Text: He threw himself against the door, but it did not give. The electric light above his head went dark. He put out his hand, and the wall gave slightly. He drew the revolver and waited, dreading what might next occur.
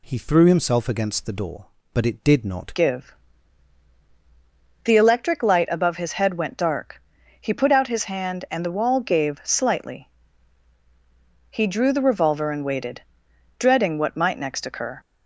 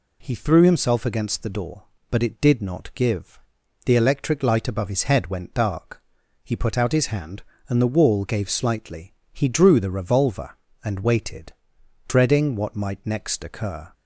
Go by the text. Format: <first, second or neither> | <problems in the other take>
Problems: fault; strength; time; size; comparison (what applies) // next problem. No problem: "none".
second | changes voice at "give"; from 2.7 s on; 12.2 s long